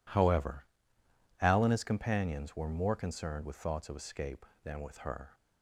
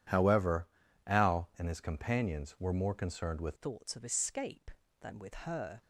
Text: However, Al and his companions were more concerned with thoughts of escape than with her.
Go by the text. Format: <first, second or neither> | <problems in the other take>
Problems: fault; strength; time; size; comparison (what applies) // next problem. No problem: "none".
first | changes voice at "thoughts"; from 3.5 s on; 2.3 s long